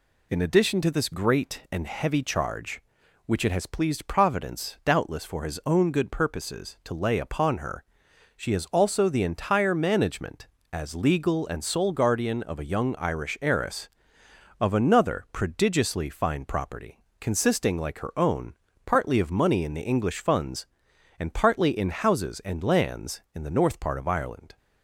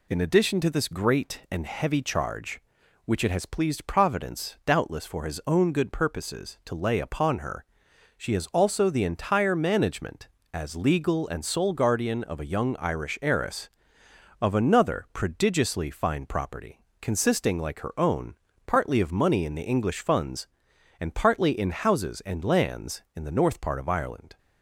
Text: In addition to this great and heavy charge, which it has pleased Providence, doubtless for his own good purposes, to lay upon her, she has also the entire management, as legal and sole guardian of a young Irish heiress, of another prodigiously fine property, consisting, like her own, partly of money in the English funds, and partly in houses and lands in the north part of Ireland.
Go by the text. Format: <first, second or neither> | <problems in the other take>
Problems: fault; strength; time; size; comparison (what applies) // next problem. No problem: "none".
neither | none